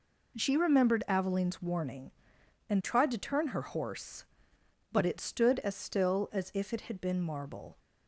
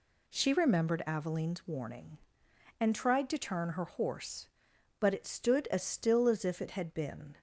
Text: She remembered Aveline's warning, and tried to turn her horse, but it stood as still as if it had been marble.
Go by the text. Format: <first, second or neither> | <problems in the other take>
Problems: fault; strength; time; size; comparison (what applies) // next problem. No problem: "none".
first | stops before "marble"; at 7.3 s